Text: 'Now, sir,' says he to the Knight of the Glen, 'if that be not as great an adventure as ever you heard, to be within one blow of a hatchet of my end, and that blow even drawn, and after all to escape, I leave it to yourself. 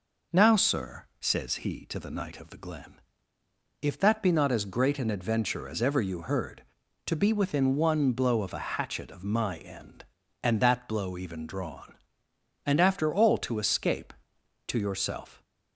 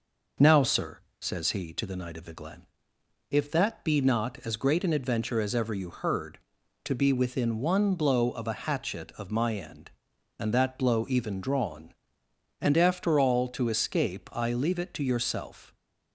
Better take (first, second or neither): second